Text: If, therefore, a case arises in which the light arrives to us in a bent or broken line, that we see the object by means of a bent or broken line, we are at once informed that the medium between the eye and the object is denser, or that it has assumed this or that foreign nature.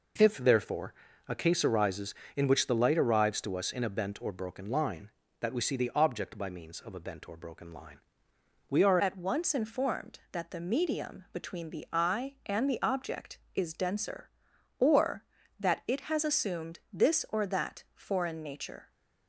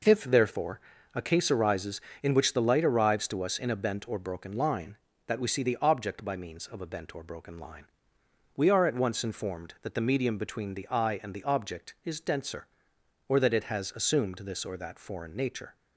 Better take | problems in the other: second | changes voice at "at"; from 9.0 s on; 9.9 s long

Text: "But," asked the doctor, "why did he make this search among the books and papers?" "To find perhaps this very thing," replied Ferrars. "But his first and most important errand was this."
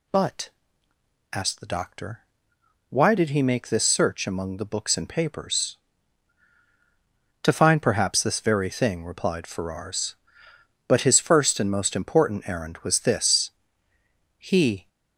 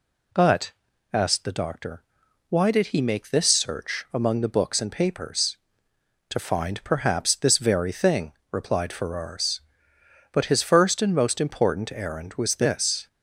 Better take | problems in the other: second | goes on to say "He"; from 14.3 s on; 0.50 s long

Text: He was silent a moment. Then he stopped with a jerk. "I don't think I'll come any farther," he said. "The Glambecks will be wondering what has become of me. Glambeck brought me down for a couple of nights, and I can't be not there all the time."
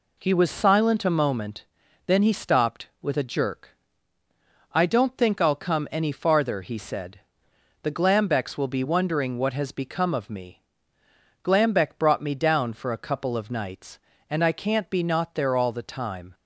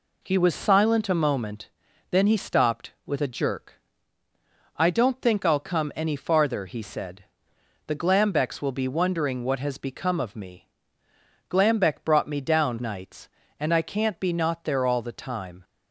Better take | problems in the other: first | skips "for a couple of"; at 12.7 s

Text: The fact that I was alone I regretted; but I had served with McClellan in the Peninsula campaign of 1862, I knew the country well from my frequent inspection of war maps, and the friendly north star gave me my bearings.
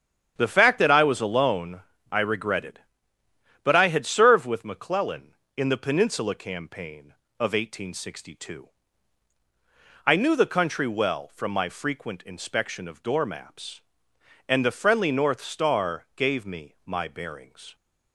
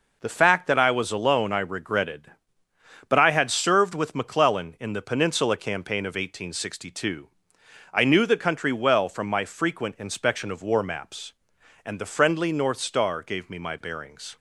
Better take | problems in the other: second | starts louder than the rest; strong; until 1.4 s; 9 dB // pauses between "alone" and "I"; slight; at 1.7 s; 0.32 s long // says "door" for "war"; at 13.0 s

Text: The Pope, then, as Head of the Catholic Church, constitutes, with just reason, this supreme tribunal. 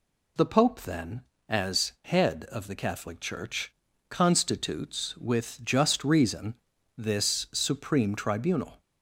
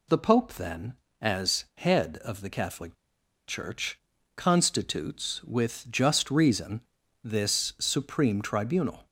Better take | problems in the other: first | pauses between "Catholic" and "Church"; noticeable; at 2.9 s; 0.53 s long

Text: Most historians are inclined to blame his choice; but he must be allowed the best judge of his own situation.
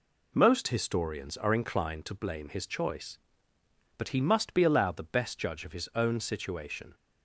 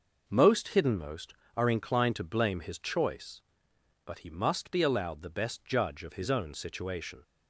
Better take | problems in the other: first | says "hiddenmost" for "historians"; at 0.7 s

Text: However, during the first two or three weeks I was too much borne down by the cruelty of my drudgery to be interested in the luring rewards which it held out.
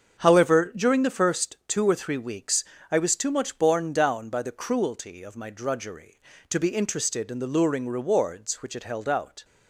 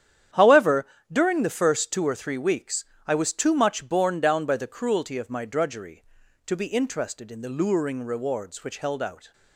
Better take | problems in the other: first | starts louder than the rest; strong; until 1.5 s; 9.5 dB; also in the first // pauses between "weeks" and "I"; slight; at 2.8 s; 0.22 s long; slight in the first // skips "it"; at 8.7 s

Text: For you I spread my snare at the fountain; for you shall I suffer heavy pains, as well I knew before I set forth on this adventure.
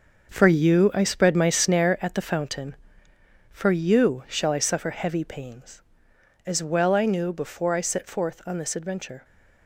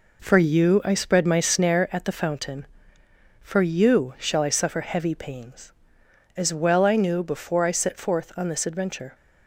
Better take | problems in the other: second | gets quieter; strong; throughout; 8.5 dB

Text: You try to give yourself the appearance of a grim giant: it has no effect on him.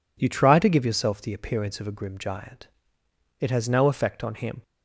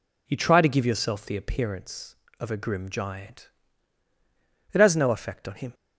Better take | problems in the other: neither | none

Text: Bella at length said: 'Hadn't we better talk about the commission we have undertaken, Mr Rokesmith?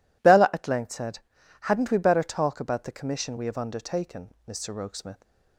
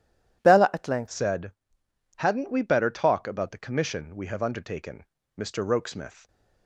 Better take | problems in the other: first | changes voice at "said"; from 1.0 s on; 5.2 s long

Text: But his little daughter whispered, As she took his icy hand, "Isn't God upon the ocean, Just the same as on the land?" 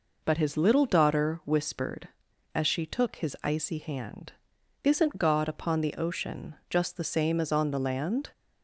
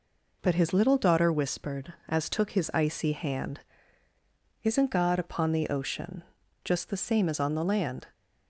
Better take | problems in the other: first | skips "she"; at 2.2 s

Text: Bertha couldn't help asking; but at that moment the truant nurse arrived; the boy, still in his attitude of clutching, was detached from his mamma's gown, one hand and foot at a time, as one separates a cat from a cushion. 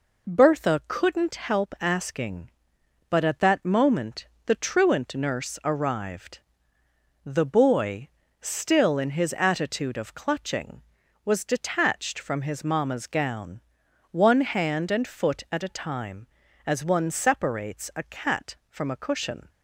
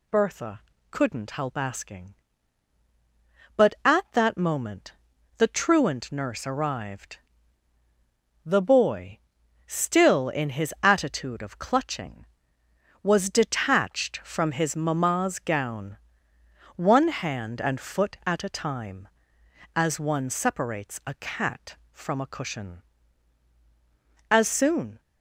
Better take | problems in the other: first | pauses between "Bertha" and "couldn't"; slight; at 0.6 s; 0.28 s long // pauses between "moment" and "the"; at 4.9 s; 0.42 s long; slight in the first // goes on to say "As soon"; noticeable; from 24.2 s on; 0.70 s long

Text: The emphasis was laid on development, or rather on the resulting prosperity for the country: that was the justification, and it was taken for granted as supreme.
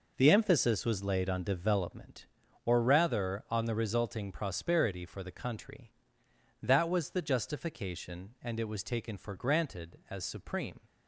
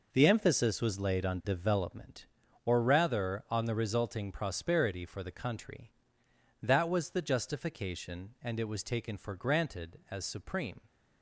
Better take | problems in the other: neither | none

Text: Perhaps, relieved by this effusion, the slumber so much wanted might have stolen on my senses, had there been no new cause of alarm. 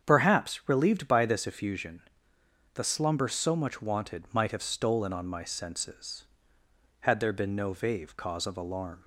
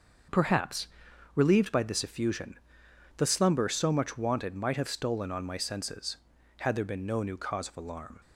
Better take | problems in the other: second | starts louder than the rest; strong; until 1.0 s; 7.5 dB; also in the second // says "vave" for "new"; at 7.7 s

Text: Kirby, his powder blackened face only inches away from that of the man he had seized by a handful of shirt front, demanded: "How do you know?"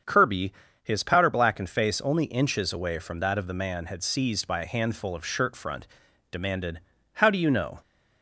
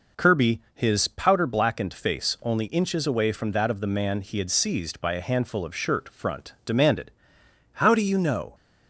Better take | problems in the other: second | starts louder than the rest; strong; until 1.3 s; 7 dB // skips "he"; at 3.8 s

